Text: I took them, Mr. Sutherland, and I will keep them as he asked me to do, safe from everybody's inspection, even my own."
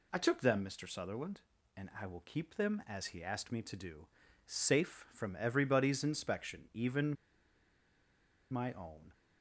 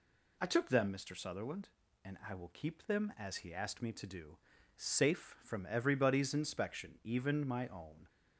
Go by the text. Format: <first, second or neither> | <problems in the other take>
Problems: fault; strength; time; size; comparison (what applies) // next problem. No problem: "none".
second | pauses between "even" and "my"; strong; at 7.1 s; 1.3 s long